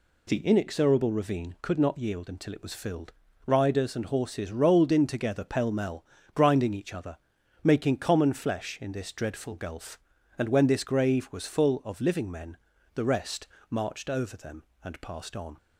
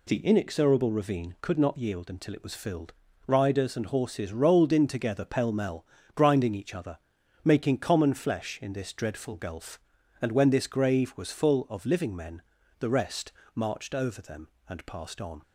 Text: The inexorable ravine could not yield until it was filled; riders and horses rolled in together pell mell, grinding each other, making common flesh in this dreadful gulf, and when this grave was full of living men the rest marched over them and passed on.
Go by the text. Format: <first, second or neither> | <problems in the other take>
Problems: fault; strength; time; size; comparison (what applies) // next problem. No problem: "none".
neither | pauses between "men" and "the"; the same in both // pauses between "rest" and "marched"; slight; the same in both